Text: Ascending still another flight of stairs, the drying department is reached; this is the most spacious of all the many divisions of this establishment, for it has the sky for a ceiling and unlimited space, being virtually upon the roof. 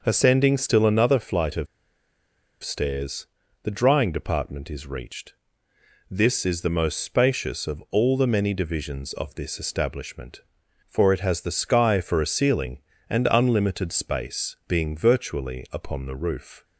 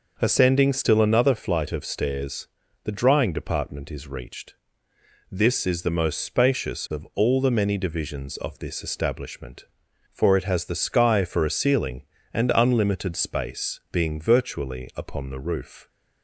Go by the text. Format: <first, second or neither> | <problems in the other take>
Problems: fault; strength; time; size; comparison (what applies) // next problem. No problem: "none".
second | starts louder than the rest; until 1.0 s; 6 dB; noticeable in the second // pauses between "of" and "stairs"; noticeable; at 1.6 s; 0.97 s long